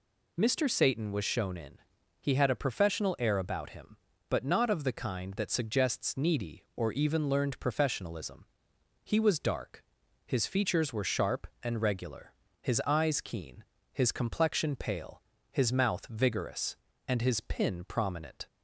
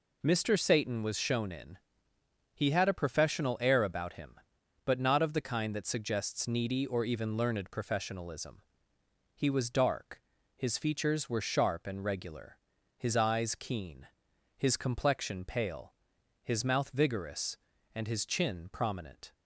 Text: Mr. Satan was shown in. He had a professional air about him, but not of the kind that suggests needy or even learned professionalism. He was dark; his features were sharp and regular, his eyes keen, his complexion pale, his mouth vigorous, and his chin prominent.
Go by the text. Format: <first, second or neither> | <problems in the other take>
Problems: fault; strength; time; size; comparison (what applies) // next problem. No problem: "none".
second | says "pin" for "chin"; at 17.4 s